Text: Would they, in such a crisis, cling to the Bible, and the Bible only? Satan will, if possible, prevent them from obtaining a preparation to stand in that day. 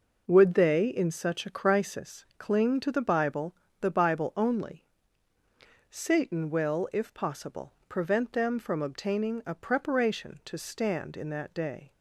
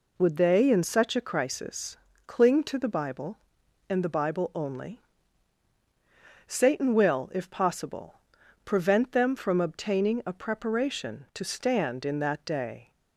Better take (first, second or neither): second